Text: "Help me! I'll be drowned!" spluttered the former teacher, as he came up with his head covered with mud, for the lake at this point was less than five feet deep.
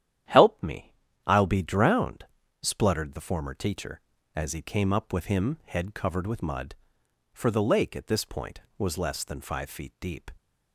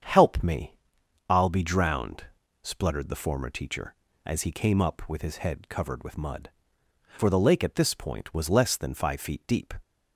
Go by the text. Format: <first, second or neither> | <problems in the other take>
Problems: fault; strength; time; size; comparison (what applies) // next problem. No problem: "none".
second | starts louder than the rest; strong; until 1.6 s; 10.5 dB; strong in the second // says "him" for "his"; at 5.2 s